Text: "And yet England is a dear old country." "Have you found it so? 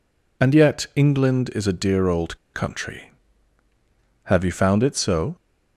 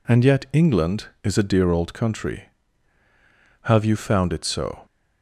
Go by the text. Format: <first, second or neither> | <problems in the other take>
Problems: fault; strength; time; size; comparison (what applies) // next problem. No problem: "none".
second | pauses between "old" and "country"; slight; at 2.3 s; 0.17 s long